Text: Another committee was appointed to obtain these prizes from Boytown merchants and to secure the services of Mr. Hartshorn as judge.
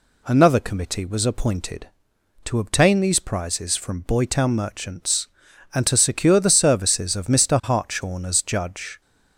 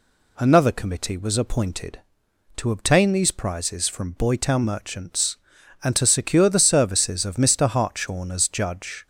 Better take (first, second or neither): neither